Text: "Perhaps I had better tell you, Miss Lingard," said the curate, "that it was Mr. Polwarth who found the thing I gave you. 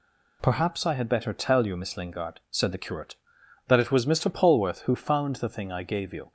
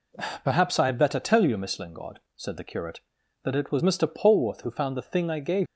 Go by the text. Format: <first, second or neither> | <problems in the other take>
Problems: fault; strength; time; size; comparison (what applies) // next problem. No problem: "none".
first | stops before "you"; at 5.6 s